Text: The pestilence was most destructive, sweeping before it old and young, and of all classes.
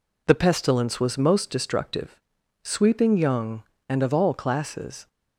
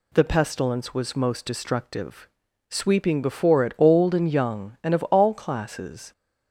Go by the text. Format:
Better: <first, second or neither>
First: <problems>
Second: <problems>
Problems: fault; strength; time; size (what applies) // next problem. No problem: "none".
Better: second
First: skips "before it old and"; at 3.1 s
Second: none